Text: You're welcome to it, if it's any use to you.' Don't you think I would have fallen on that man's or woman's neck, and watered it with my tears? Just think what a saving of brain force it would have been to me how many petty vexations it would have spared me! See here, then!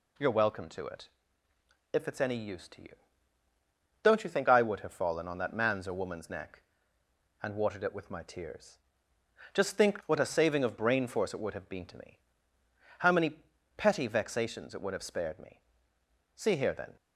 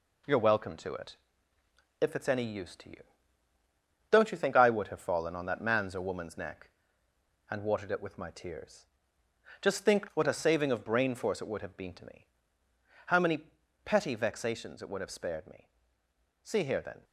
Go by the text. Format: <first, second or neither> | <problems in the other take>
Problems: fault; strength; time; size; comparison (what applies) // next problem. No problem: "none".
first | gets quieter; slight; throughout; 3 dB // pauses between "me" and "how"; noticeable; at 12.2 s; 0.82 s long; noticeable in the first // pauses between "many" and "petty"; at 13.3 s; 0.44 s long; also in the first